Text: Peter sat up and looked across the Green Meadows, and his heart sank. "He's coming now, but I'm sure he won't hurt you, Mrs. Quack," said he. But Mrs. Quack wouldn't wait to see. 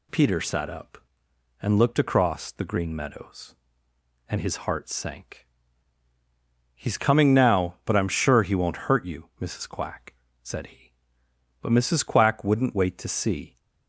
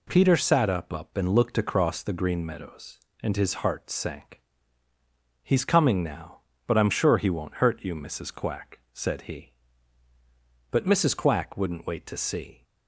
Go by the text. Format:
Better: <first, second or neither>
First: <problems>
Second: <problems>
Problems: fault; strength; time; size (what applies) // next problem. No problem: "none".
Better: first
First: none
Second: says "up" twice; at 0.9 s